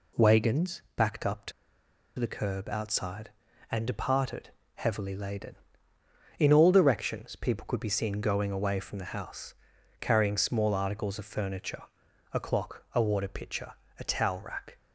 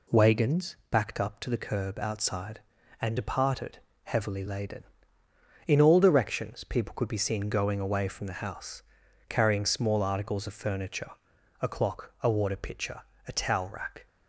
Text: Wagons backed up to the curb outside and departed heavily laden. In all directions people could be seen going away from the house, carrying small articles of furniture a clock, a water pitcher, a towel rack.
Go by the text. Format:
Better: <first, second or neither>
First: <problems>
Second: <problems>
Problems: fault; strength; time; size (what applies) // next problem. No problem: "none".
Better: second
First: pauses between "to" and "the"; noticeable; at 1.5 s; 0.67 s long // pauses between "departed" and "heavily"; slight; at 4.4 s; 0.26 s long // pauses between "furniture" and "a"; noticeable; at 11.8 s; 0.50 s long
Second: pauses between "departed" and "heavily"; slight; at 3.7 s; 0.26 s long // pauses between "furniture" and "a"; noticeable; at 11.0 s; 0.50 s long